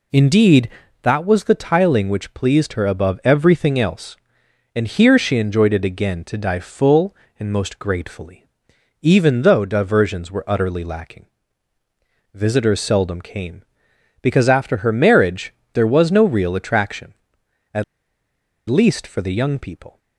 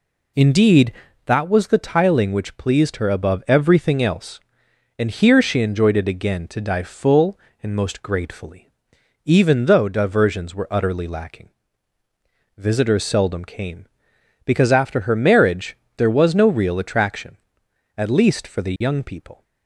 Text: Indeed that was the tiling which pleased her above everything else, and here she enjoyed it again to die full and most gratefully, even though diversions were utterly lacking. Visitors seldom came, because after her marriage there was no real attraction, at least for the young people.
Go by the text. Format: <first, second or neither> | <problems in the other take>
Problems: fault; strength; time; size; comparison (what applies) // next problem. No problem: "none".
second | pauses between "marriage" and "there"; slight; at 15.5 s; 0.20 s long; slight in the second // pauses between "at" and "least"; noticeable; at 17.8 s; 0.86 s long